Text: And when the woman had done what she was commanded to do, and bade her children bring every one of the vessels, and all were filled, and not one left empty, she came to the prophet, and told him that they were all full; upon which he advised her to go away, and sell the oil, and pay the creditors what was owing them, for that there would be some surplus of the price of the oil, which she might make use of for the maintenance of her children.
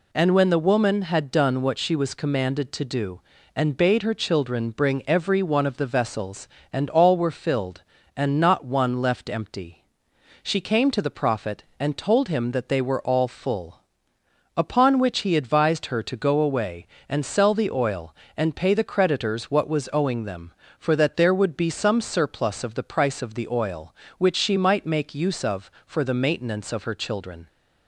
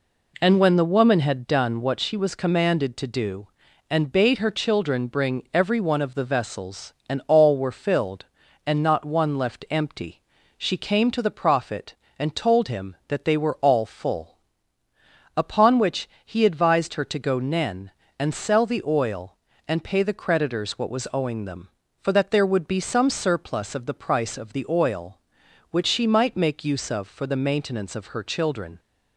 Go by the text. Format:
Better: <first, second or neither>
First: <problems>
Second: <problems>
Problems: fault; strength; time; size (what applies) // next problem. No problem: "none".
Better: first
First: none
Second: pauses between "which" and "he"; slight; at 16.0 s; 0.16 s long // says "nen" for "away"; at 17.3 s